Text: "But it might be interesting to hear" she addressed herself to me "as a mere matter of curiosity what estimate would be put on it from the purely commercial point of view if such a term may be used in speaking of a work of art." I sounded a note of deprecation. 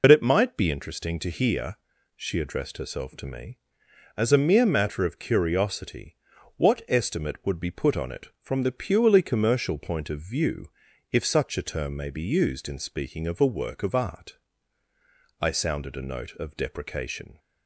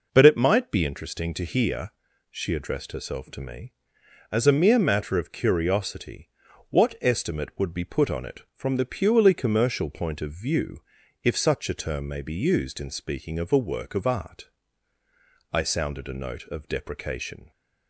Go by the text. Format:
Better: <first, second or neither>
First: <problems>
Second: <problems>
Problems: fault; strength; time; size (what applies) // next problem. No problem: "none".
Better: second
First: loses the start of "But"; at 0.0 s; 70 ms // pauses between "hear" and "she"; at 1.7 s; 0.40 s long // pauses between "curiosity" and "what"; at 6.1 s; 0.40 s long // pauses between "view" and "if"; at 10.6 s; 0.44 s long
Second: pauses between "hear" and "she"; at 1.9 s; 0.40 s long // pauses between "curiosity" and "what"; at 6.3 s; 0.40 s long // pauses between "view" and "if"; at 10.8 s; 0.44 s long